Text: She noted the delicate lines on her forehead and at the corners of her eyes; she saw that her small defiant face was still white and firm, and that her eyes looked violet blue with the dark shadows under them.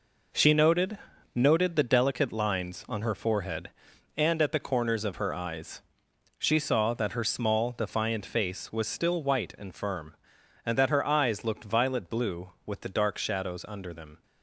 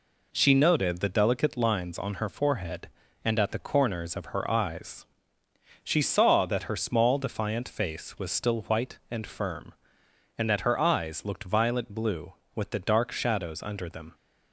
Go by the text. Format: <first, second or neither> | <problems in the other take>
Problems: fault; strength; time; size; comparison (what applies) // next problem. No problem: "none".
second | says "noted" twice; at 1.3 s